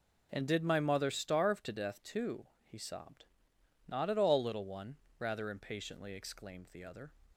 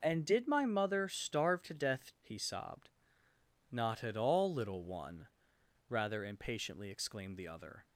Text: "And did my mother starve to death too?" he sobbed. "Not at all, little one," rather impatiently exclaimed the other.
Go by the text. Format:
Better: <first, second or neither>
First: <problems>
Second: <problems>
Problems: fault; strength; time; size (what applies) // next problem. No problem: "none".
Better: first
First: none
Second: skips "too"; at 2.1 s